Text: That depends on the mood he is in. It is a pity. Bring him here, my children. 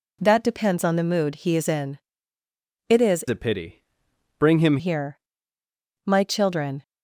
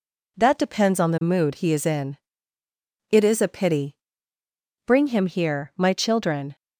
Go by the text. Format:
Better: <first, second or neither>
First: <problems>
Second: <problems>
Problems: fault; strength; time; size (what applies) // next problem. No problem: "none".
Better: second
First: changes voice from "a" to "him"; from 3.2 to 4.7 s; 1.5 s long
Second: none